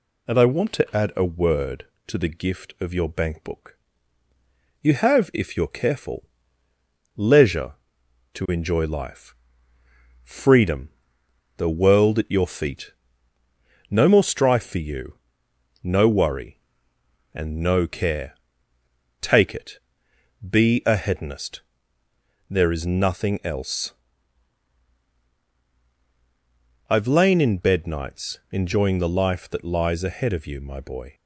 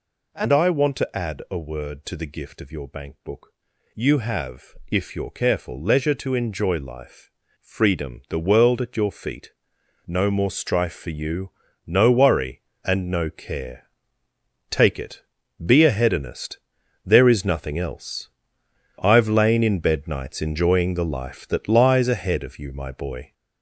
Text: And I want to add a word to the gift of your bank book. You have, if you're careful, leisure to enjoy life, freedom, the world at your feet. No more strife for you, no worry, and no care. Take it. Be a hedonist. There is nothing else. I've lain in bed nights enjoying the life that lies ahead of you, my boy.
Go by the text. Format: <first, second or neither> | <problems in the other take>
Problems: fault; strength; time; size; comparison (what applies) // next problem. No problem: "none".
first | gets louder; noticeable; throughout; 5.5 dB